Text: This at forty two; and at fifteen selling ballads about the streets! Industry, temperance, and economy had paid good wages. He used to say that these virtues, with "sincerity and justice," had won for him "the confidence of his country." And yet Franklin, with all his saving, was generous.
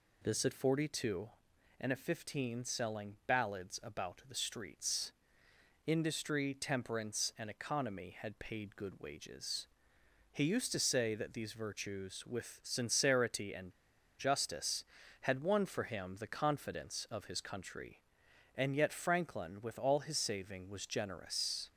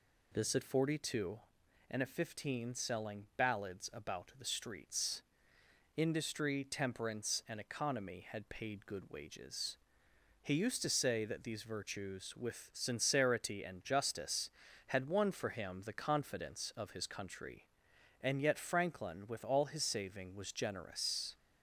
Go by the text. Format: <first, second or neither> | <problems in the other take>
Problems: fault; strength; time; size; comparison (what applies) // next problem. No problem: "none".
second | pauses between "and" and "justice"; noticeable; at 13.7 s; 0.47 s long